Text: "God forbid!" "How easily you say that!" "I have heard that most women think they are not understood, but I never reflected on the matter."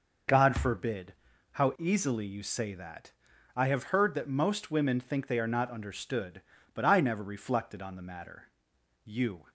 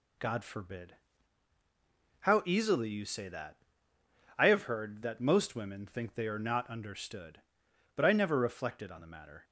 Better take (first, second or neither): second